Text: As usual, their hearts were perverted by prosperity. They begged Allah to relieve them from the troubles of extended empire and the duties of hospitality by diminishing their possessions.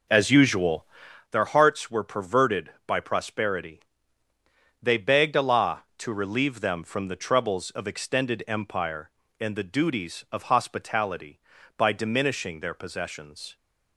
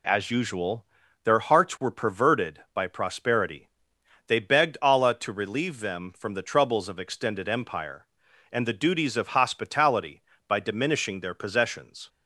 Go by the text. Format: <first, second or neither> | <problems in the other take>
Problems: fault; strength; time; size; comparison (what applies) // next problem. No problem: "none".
second | starts louder than the rest; noticeable; until 1.2 s; 5 dB